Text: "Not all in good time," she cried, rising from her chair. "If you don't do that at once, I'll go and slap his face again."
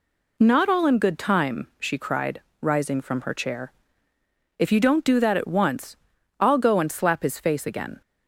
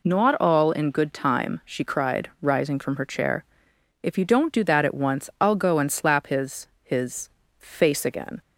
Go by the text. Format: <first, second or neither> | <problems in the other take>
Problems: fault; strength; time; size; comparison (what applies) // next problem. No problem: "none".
first | says "his" twice; at 6.8 s